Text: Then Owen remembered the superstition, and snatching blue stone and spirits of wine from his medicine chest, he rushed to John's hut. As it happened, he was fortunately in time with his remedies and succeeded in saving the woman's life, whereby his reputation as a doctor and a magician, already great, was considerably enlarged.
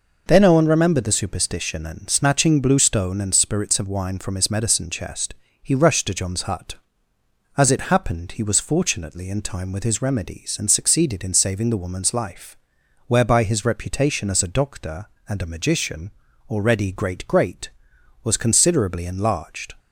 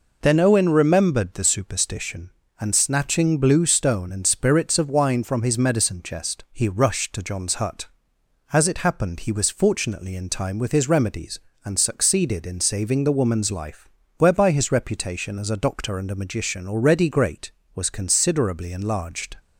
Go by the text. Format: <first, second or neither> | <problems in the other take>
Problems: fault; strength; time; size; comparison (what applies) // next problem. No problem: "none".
second | says "great" twice; at 17.2 s